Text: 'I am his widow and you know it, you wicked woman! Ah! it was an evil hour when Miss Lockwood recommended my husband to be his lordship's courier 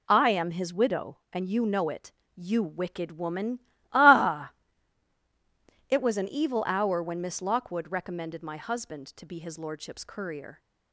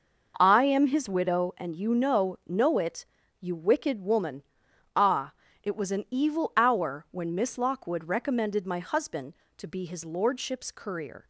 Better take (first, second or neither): first